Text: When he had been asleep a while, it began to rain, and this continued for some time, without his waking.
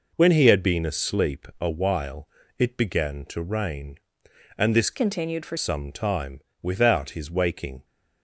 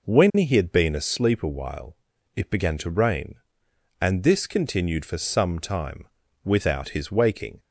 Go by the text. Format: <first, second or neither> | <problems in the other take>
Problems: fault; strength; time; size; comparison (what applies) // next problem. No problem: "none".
second | changes voice from "continued" to "for"; from 4.9 to 5.5 s; 0.6 s long